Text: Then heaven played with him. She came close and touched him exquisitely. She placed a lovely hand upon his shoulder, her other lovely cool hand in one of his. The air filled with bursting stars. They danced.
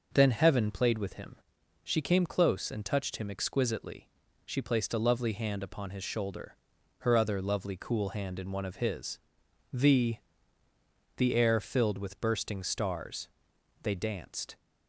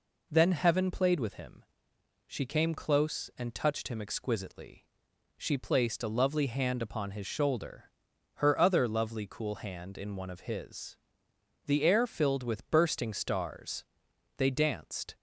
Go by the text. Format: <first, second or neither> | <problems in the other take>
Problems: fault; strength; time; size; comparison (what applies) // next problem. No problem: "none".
second | says "The" twice; at 11.1 s